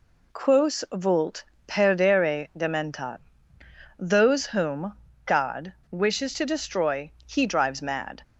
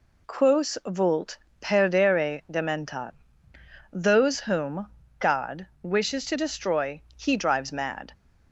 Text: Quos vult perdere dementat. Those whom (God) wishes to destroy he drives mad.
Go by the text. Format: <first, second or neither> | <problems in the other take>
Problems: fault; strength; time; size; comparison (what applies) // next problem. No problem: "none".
neither | pauses between "vult" and "perdere"; slight; the same in both // pauses between "destroy" and "he"; slight; the same in both